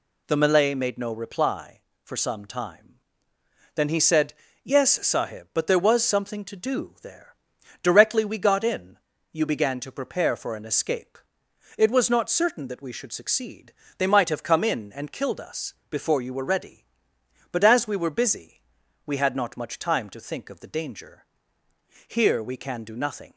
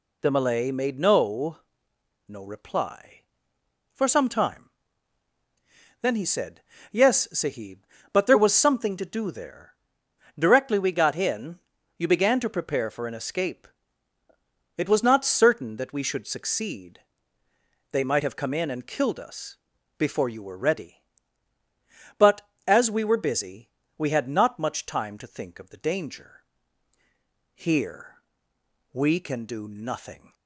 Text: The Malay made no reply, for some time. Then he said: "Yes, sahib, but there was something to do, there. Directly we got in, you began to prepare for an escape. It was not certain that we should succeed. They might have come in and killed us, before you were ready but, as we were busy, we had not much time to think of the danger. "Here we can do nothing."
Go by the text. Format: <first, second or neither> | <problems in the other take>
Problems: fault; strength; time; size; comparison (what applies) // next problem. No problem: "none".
first | says "no" twice; at 2.2 s // pauses between "Here" and "we"; noticeable; at 28.2 s; 0.70 s long